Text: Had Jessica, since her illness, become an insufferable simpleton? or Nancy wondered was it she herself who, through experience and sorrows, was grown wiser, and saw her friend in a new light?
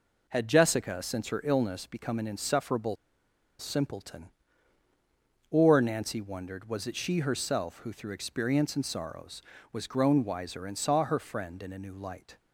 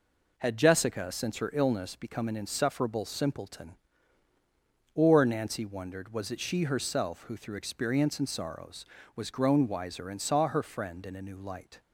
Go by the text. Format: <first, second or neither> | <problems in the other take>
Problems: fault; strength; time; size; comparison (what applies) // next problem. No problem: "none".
second | pauses between "insufferable" and "simpleton"; noticeable; at 2.9 s; 0.63 s long